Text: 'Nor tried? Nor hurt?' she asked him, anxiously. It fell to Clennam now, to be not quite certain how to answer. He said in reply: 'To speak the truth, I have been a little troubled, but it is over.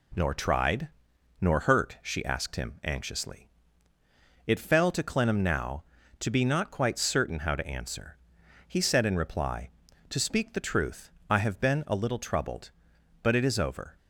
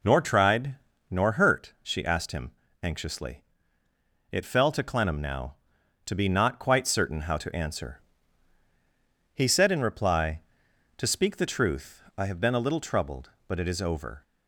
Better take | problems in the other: neither | none

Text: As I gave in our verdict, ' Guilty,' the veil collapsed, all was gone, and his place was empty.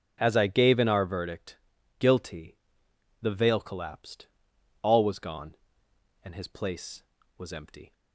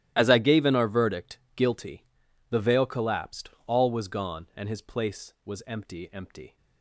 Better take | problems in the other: first | starts louder than the rest; strong; until 1.1 s; 12.5 dB; also in the first // says "empty" twice; at 6.1 s

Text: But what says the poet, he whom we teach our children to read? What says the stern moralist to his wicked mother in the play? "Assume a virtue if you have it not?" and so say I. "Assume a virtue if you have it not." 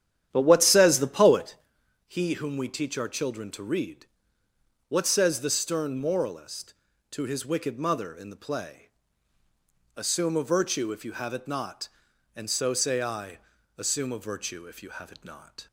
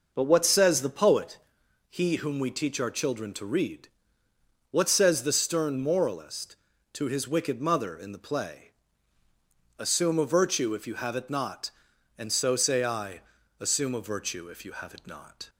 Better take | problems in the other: second | starts louder than the rest; strong; until 1.6 s; 10.5 dB

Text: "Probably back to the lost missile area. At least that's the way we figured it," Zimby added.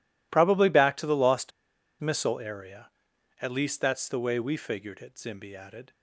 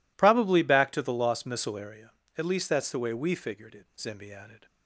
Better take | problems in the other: second | pauses between "lost" and "missile"; noticeable; at 1.5 s; 0.50 s long

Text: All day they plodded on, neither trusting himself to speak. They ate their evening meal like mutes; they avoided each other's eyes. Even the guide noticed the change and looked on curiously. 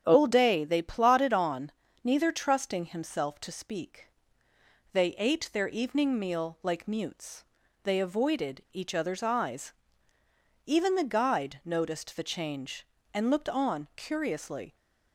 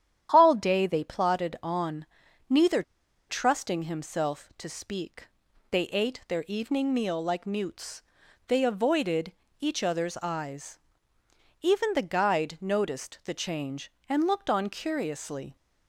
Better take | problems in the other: first | starts louder than the rest; strong; until 1.3 s; 10 dB; strong in the first // pauses between "neither" and "trusting"; noticeable; at 2.8 s; 0.47 s long // pauses between "avoided" and "each"; slight; at 9.3 s; 0.30 s long

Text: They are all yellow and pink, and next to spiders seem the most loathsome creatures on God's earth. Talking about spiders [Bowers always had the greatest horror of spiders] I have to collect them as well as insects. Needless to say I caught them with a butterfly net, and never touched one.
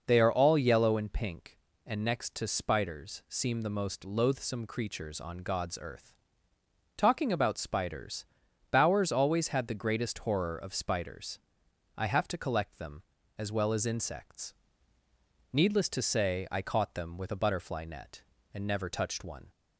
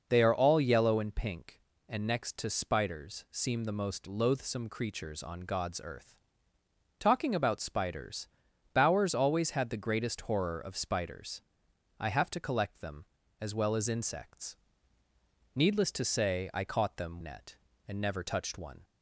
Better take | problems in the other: first | pauses between "spiders" and "Bowers"; noticeable; at 8.2 s; 0.46 s long; noticeable in the first // pauses between "spiders" and "I"; noticeable; at 11.4 s; 0.58 s long; noticeable in the first // skips "with a butterfly"; at 17.1 s

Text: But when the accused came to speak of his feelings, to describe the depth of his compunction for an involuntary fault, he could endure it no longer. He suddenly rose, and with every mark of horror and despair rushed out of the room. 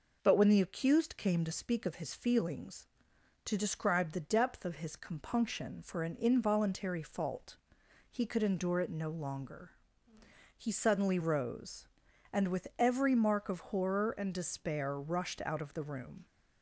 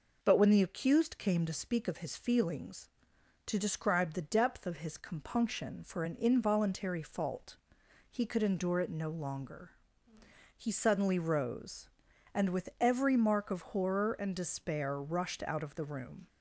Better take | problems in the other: neither | none

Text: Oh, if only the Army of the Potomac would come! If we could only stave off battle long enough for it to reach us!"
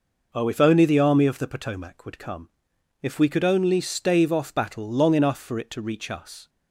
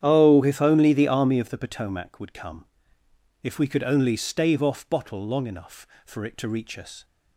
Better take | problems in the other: first | starts louder than the rest; strong; until 1.0 s; 9.5 dB // says "bottle" for "battle"; at 4.8 s

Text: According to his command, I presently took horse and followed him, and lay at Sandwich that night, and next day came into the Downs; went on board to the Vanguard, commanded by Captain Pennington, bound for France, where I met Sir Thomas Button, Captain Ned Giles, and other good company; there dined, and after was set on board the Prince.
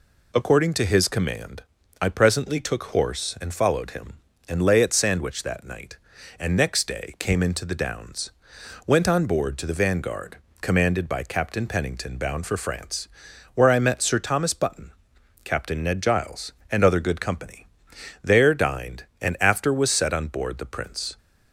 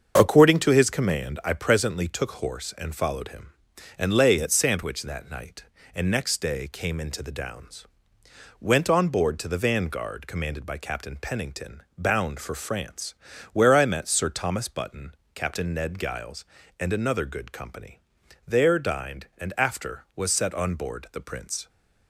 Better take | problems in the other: first | starts louder than the rest; until 1.1 s; 6.5 dB // says "another" for "other"; at 16.9 s

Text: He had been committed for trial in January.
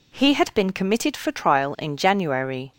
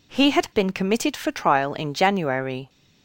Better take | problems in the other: neither | none

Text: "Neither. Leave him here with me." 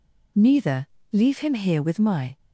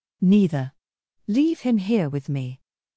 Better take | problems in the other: second | says "my" for "me"; at 1.9 s

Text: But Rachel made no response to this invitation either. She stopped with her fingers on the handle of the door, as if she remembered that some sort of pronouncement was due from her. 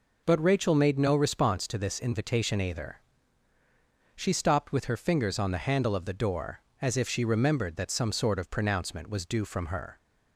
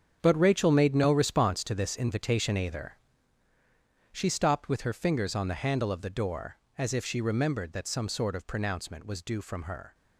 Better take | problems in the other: first | gets quieter; strong; throughout; 11 dB

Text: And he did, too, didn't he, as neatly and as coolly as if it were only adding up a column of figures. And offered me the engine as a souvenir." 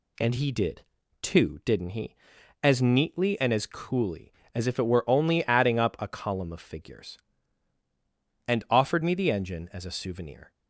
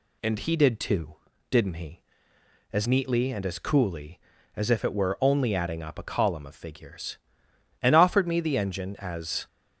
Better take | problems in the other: first | stops before "a souvenir"; at 9.4 s

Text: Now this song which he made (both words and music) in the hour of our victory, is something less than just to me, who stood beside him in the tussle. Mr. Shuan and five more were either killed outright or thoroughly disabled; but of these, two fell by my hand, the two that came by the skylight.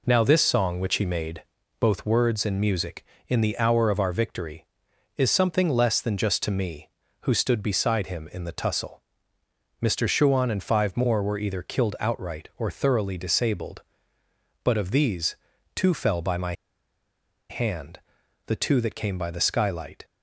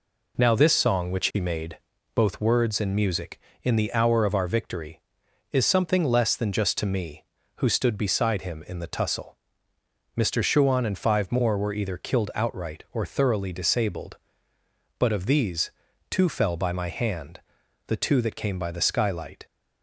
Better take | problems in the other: second | pauses between "my" and "hand"; noticeable; at 16.5 s; 0.97 s long

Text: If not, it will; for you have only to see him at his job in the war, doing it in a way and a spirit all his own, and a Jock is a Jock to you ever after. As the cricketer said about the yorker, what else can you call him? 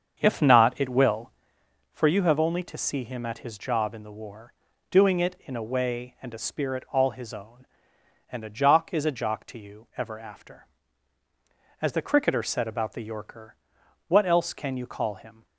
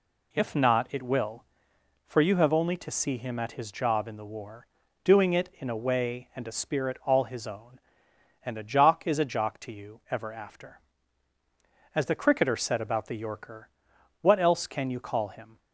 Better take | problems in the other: second | starts louder than the rest; until 1.5 s; 7 dB

